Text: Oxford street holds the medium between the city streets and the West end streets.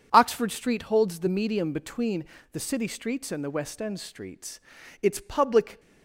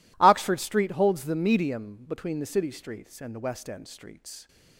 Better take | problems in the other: second | pauses between "between" and "the"; slight; at 2.2 s; 0.28 s long // goes on to say "Its public"; noticeable; from 5.0 s on; 0.78 s long

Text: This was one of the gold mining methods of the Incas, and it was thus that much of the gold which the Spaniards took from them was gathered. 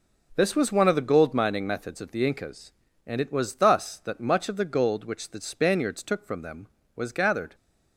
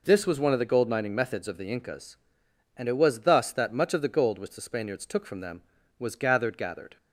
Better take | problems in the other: first | says "gathered" twice; at 6.5 s

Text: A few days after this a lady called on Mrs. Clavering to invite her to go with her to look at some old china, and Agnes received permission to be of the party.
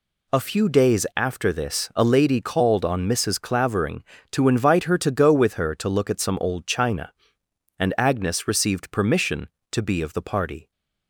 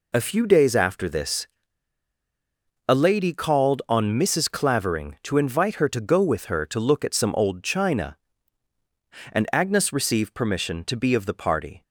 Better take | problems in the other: first | pauses between "this" and "a"; strong; at 1.4 s; 1.3 s long

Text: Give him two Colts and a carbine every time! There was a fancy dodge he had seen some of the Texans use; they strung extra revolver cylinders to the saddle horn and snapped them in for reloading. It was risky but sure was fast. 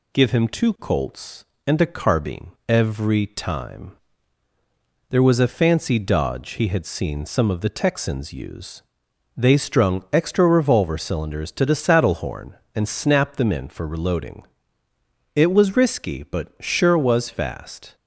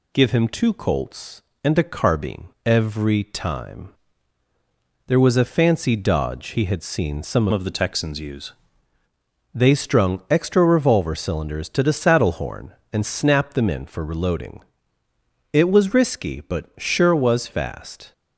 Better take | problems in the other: first | pauses between "carbine" and "every"; slight; at 2.4 s; 0.18 s long; slight in the first // changes voice from "of" to "use"; from 7.5 to 8.5 s; 1.0 s long

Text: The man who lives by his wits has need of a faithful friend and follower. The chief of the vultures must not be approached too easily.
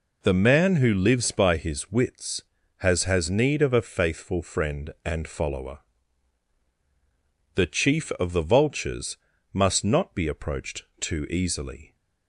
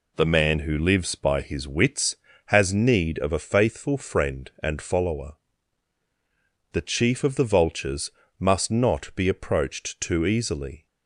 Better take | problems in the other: second | says "has" twice; at 3.0 s // pauses between "vultures" and "must"; slight; at 9.1 s; 0.36 s long; slight in the second // pauses between "approached" and "too"; slight; at 10.8 s; 0.16 s long

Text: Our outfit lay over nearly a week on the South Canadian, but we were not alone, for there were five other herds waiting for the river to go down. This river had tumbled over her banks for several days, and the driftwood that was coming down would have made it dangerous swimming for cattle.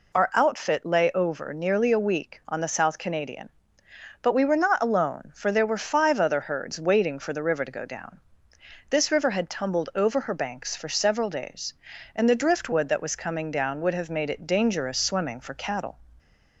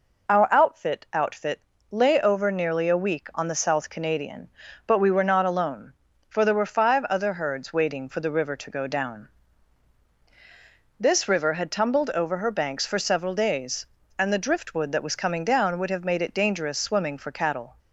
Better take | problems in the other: first | says "outfit" twice; at 1.1 s

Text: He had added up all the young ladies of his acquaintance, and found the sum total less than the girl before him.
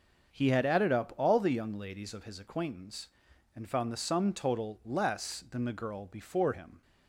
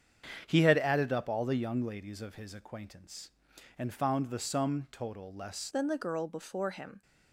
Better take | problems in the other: first | starts louder than the rest; strong; until 1.4 s; 7.5 dB; also in the first // changes voice at "than"; from 5.7 s on; 1.3 s long

